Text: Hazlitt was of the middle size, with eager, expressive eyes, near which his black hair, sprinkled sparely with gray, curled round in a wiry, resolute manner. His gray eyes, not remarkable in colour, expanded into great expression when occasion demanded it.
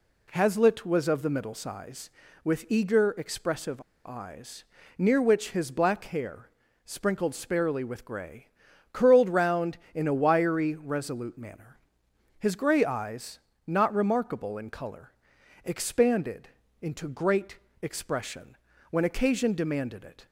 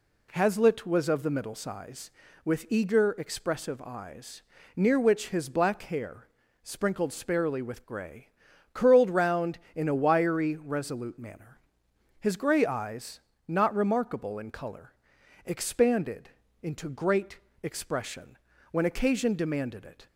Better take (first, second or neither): second